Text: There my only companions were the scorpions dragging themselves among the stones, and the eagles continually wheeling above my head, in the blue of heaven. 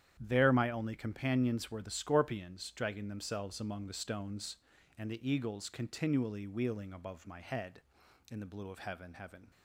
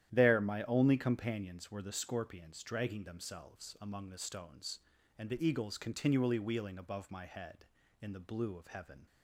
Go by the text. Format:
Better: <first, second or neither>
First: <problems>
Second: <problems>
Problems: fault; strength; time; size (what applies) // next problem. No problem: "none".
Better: second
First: starts louder than the rest; strong; until 1.2 s; 10 dB // says "heaven" twice; at 9.1 s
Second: starts louder than the rest; strong; until 1.1 s; 11.5 dB